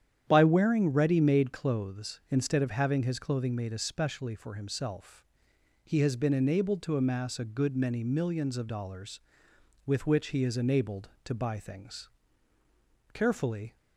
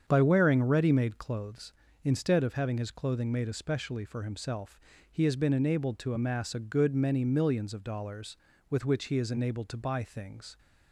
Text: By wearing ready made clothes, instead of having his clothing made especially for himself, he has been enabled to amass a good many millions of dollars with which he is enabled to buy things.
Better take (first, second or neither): second